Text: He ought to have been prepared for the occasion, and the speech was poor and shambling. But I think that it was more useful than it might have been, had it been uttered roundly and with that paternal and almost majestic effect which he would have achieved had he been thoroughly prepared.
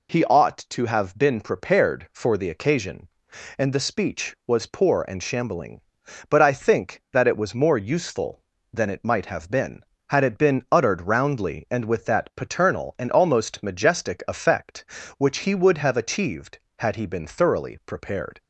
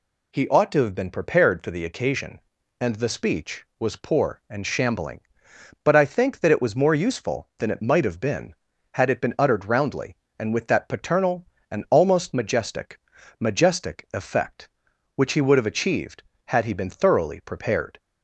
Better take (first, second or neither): first